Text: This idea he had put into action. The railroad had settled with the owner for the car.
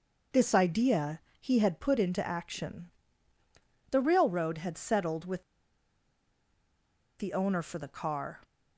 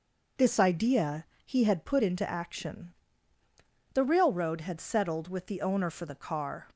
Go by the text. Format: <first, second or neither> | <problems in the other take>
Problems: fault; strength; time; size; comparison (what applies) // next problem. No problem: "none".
second | pauses between "idea" and "he"; slight; at 1.1 s; 0.20 s long; slight in the second // pauses between "with" and "the"; strong; at 5.4 s; 1.7 s long